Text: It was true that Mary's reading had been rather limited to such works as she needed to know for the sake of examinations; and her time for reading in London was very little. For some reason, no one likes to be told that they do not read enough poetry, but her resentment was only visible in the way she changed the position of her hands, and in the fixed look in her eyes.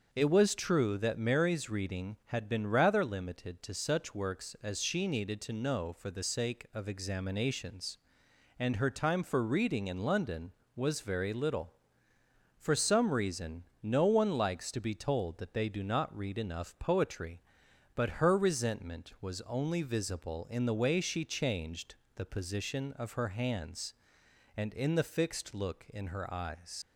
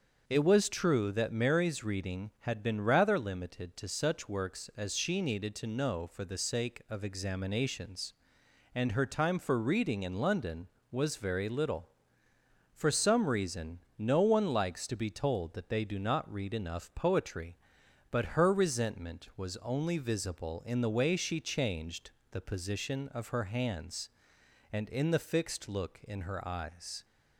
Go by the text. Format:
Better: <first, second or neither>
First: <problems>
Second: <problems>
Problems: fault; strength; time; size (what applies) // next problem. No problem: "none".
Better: second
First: starts louder than the rest; until 1.1 s; 6.5 dB // pauses between "changed" and "the"; slight; at 21.9 s; 0.22 s long // leaves "eyes" unfinished; at 26.8 s; 80 ms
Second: starts louder than the rest; until 1.2 s; 6.5 dB // pauses between "changed" and "the"; slight; at 22.0 s; 0.22 s long